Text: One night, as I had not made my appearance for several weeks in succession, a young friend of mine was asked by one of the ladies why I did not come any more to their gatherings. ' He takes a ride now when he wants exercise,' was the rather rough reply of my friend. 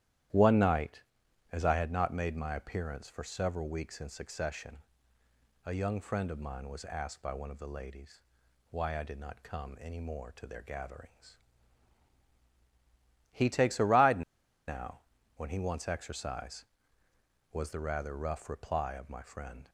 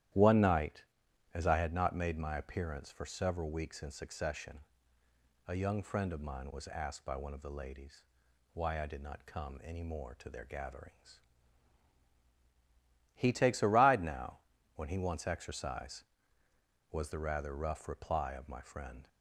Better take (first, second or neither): second